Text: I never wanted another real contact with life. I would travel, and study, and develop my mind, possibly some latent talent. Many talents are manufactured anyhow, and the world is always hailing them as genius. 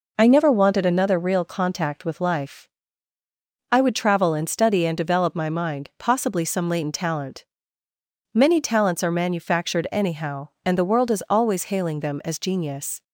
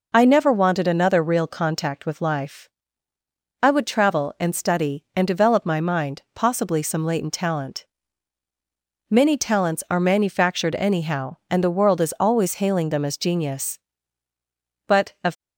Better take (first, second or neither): first